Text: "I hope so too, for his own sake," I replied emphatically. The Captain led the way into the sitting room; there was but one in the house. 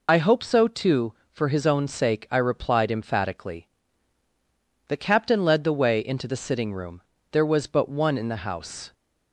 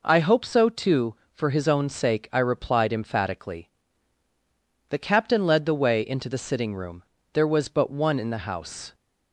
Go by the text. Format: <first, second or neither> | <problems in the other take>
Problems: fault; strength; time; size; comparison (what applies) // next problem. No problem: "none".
second | loses the start of "I"; at 0.0 s; 55 ms